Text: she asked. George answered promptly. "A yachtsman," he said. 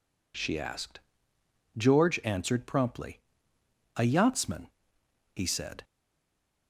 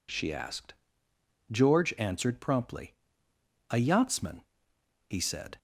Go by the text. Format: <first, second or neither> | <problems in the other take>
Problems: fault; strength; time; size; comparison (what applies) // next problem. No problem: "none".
second | stays silent after the last word; slight; from 5.8 s on; 0.8 s long